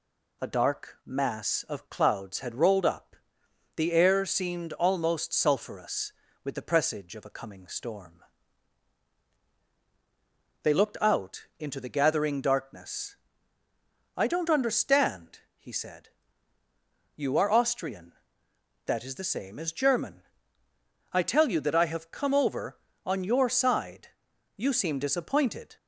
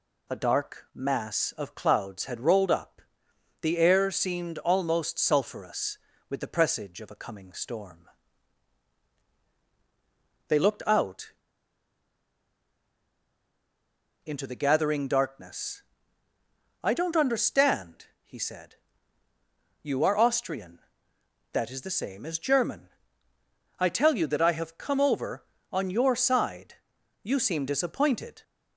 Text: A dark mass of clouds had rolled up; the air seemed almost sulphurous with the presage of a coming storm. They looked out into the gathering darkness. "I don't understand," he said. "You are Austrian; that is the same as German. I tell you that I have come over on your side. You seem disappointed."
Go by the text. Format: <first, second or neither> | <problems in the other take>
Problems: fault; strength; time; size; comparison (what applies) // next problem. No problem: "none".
first | pauses between "out" and "into"; strong; at 11.3 s; 2.9 s long